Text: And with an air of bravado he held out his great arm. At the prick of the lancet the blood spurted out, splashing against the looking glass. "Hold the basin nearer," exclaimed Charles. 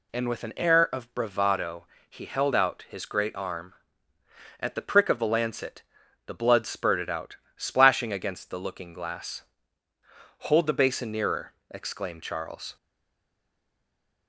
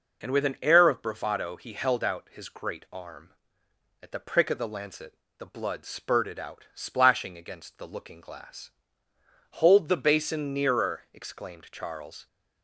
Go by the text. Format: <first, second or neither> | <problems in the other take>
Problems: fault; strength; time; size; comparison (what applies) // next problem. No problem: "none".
second | pauses between "bravado" and "he"; slight; at 1.8 s; 0.24 s long // pauses between "lancet" and "the"; at 5.8 s; 0.44 s long; slight in the second // stays silent after the last word; noticeable; from 12.7 s on; 1.5 s long